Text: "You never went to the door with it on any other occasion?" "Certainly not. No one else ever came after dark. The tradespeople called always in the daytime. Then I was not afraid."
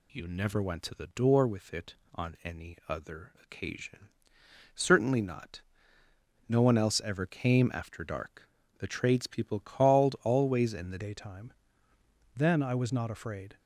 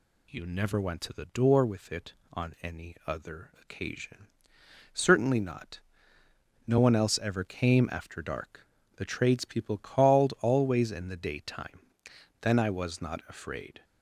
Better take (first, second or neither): second